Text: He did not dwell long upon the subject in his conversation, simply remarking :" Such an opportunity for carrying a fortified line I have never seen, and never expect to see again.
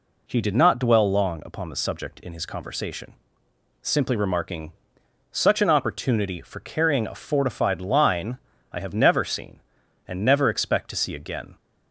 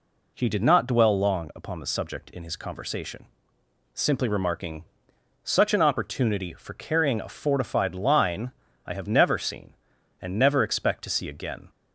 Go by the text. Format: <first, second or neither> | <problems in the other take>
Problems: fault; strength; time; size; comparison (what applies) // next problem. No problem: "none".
neither | pauses between "line" and "I"; slight; the same in both